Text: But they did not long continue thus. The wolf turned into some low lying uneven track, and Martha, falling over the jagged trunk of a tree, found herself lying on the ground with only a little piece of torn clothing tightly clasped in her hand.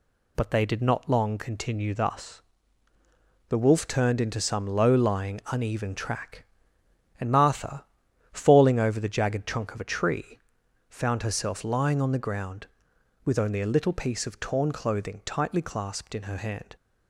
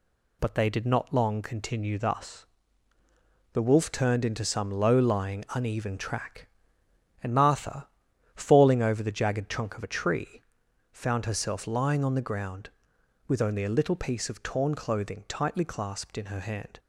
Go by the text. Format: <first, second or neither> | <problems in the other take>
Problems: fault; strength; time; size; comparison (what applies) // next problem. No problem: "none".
neither | none